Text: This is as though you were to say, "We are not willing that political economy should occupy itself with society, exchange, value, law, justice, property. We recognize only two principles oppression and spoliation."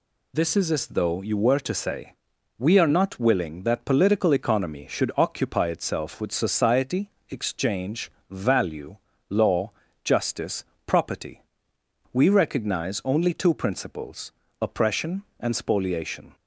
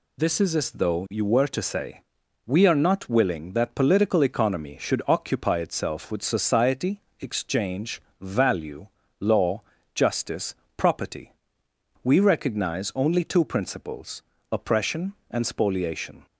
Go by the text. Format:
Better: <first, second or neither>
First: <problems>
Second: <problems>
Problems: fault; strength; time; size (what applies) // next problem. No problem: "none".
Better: neither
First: pauses between "principles" and "oppression"; slight; at 14.3 s; 0.30 s long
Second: pauses between "principles" and "oppression"; slight; at 14.2 s; 0.30 s long